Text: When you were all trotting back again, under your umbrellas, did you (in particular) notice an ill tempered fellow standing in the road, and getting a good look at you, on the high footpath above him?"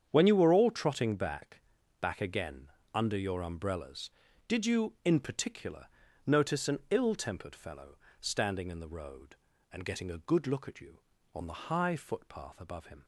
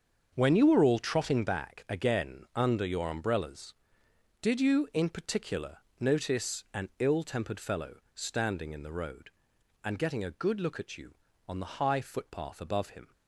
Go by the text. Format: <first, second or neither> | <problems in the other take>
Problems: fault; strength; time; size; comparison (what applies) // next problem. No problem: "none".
second | starts louder than the rest; strong; until 1.1 s; 8 dB; also in the second // says "back" twice; at 2.0 s // pauses between "fellow" and "standing"; slight; at 7.9 s; 0.20 s long; slight in the second